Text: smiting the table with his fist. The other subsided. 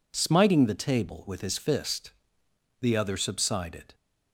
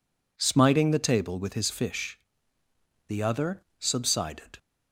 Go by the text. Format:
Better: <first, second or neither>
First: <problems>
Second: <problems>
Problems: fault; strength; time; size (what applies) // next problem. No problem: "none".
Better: first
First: none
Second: says "fish" for "fist"; at 1.6 s // pauses between "other" and "subsided"; slight; at 3.6 s; 0.18 s long